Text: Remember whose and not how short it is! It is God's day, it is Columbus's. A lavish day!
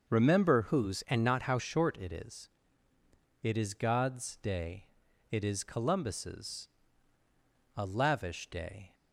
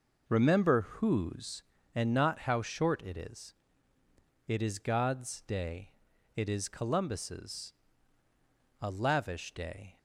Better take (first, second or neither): second